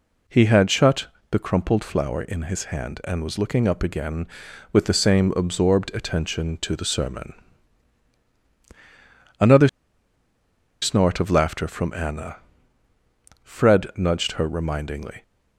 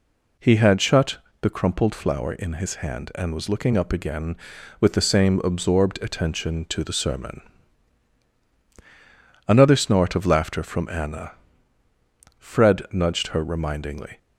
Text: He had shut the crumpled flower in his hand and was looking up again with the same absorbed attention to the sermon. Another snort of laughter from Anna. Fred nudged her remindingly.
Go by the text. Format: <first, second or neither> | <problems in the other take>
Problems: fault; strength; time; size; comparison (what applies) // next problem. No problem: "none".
second | pauses between "shut" and "the"; slight; at 1.0 s; 0.22 s long; slight in the second // pauses between "Another" and "snort"; at 9.6 s; 1.1 s long